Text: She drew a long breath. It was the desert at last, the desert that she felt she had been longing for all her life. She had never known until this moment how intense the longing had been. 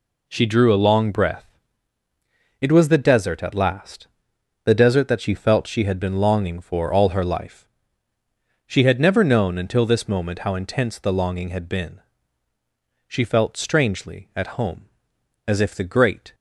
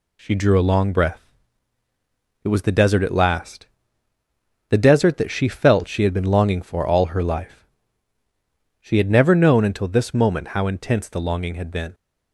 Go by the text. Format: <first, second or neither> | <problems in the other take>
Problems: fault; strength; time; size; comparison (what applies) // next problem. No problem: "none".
second | goes on to say "She felt strangely at home as if the great"; strong; from 13.0 s on; 3.2 s long